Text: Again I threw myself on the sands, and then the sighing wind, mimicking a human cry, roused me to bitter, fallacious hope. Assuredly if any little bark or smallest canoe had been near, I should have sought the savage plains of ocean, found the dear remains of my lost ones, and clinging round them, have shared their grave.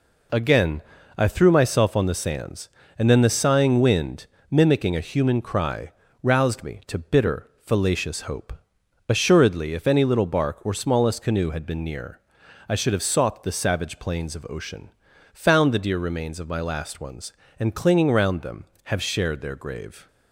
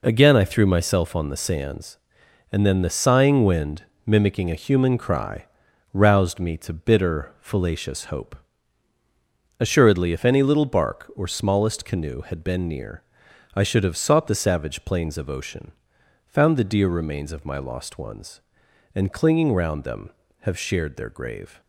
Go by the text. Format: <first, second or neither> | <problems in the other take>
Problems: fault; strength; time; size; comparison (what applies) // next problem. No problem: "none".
second | pauses between "Again" and "I"; slight; at 0.8 s; 0.36 s long // says "last" for "lost"; at 16.6 s